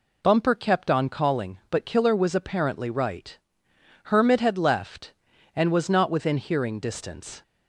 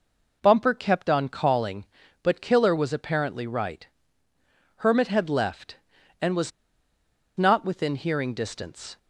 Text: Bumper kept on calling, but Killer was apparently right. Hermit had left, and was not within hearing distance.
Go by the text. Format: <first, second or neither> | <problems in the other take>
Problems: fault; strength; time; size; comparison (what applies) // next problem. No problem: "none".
first | pauses between "was" and "not"; noticeable; at 6.5 s; 0.86 s long